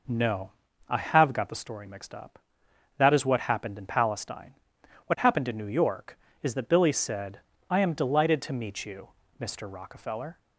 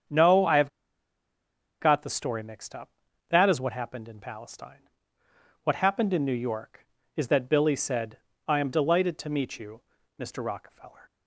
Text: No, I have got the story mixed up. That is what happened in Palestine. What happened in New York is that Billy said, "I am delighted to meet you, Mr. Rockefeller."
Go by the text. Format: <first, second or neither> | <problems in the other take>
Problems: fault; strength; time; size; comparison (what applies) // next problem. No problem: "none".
first | starts louder than the rest; strong; until 2.2 s; 7.5 dB // pauses between "have" and "got"; at 0.6 s; 1.1 s long